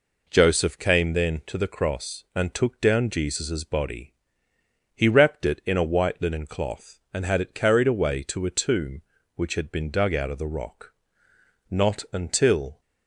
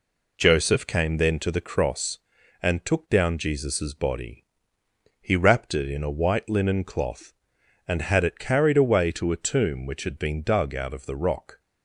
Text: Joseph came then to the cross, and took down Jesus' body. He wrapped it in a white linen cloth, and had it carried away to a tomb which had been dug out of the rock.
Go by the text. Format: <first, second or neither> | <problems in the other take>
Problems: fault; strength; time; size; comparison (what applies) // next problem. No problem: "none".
second | goes on to say "Not until"; noticeable; from 11.6 s on; 1.1 s long